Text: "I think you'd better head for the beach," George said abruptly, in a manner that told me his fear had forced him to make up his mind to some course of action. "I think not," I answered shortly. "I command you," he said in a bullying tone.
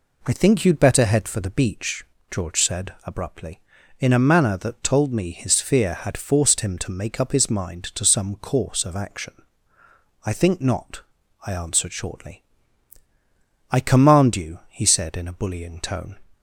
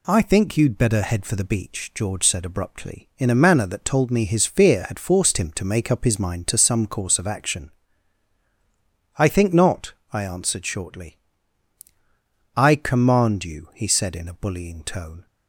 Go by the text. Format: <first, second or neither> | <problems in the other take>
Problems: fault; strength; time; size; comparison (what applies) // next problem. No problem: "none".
neither | none